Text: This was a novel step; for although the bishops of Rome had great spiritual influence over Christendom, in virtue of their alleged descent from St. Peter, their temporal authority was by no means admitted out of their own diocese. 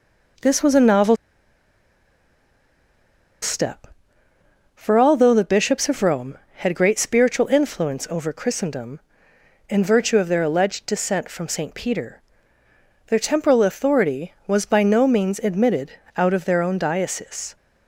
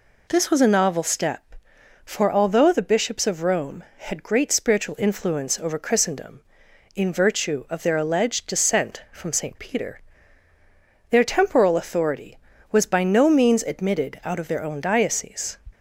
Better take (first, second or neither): second